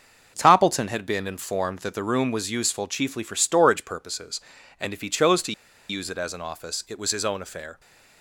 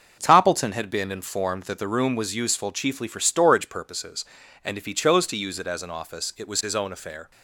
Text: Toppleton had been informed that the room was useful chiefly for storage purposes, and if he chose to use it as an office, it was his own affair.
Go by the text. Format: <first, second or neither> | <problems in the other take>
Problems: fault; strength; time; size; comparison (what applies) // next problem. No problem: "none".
second | starts louder than the rest; noticeable; until 1.3 s; 6 dB; noticeable in the second // pauses between "to" and "use"; at 5.5 s; 0.36 s long